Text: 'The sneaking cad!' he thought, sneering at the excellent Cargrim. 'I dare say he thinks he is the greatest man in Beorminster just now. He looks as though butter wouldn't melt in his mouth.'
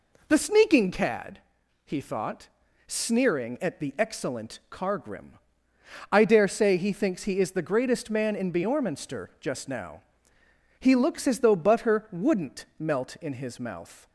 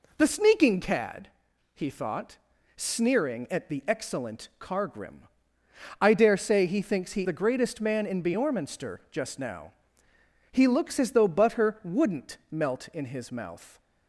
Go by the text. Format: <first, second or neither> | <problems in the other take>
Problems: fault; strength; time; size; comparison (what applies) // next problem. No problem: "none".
first | skips "is"; at 7.2 s